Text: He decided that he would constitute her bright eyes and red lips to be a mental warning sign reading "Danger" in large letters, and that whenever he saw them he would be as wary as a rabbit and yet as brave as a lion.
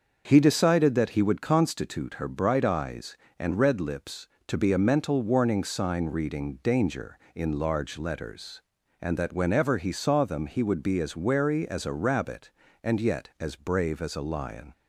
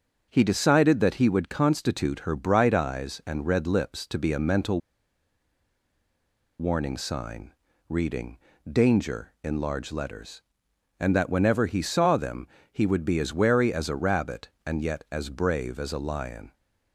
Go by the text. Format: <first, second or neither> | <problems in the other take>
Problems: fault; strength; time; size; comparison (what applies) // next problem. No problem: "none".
first | starts louder than the rest; until 1.3 s; 6 dB; also in the first // pauses between "mental" and "warning"; strong; at 4.8 s; 1.8 s long // pauses between "sign" and "reading"; slight; at 7.5 s; 0.36 s long // pauses between "reading" and "Danger"; slight; at 8.3 s; 0.32 s long // pauses between "them" and "he"; slight; at 12.4 s; 0.24 s long